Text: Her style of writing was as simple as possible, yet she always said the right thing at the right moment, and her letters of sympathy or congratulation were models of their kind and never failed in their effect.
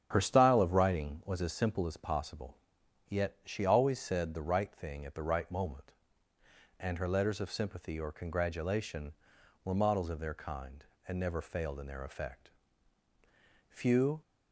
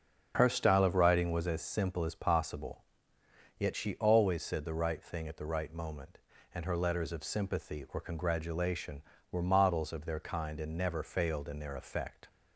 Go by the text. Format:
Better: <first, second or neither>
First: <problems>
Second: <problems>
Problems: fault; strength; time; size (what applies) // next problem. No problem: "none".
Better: second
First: starts louder than the rest; strong; until 1.1 s; 8 dB // goes on to say "Few"; from 13.6 s on; 0.52 s long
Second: starts louder than the rest; until 1.3 s; 6.5 dB